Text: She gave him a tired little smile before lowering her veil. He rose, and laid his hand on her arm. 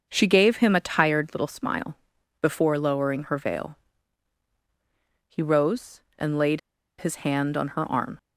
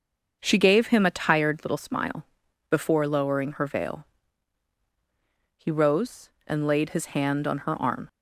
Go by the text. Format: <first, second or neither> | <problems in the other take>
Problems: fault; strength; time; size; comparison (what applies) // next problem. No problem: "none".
second | starts louder than the rest; until 1.0 s; 6.5 dB; also in the second // pauses between "smile" and "before"; noticeable; at 1.9 s; 0.46 s long; noticeable in the second // pauses between "laid" and "his"; at 6.5 s; 0.39 s long